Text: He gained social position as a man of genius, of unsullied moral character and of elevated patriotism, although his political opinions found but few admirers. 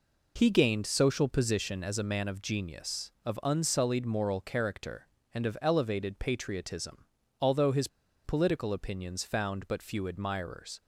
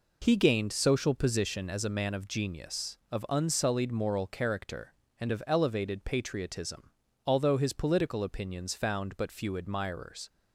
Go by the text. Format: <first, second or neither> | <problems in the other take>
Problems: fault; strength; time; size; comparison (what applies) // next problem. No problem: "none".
second | pauses between "his" and "political"; at 7.8 s; 0.37 s long